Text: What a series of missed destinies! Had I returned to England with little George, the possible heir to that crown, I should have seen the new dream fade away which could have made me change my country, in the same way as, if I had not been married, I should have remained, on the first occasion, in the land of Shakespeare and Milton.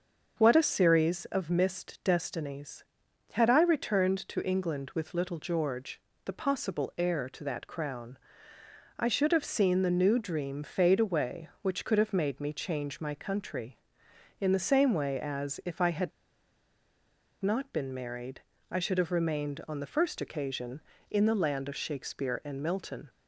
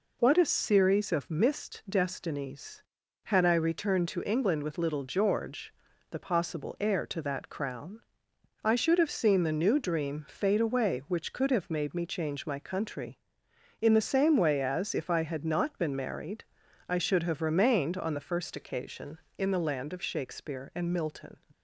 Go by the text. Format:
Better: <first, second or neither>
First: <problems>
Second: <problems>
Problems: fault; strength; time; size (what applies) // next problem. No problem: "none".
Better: second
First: starts louder than the rest; until 1.3 s; 6 dB // pauses between "had" and "not"; strong; at 16.1 s; 1.3 s long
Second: none